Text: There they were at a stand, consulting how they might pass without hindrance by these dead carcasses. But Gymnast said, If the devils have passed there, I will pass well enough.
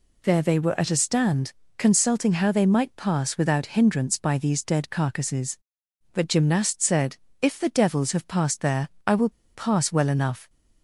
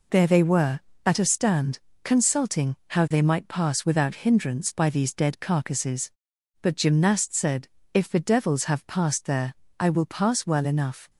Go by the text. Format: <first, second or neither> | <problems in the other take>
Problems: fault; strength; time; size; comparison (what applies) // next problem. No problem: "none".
second | pauses between "will" and "pass"; slight; at 9.2 s; 0.24 s long